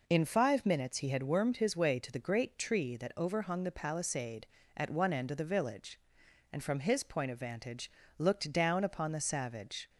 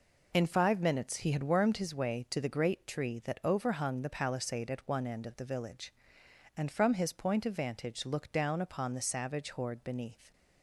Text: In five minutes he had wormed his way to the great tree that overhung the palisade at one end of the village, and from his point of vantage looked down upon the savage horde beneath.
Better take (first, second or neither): second